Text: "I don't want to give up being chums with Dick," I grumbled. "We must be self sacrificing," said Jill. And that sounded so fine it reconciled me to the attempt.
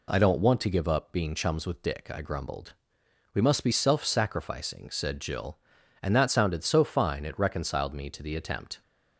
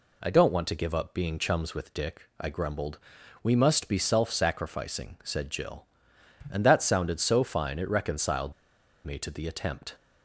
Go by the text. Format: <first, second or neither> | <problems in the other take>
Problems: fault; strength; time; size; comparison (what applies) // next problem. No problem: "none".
first | pauses between "reconciled" and "me"; noticeable; at 8.5 s; 0.53 s long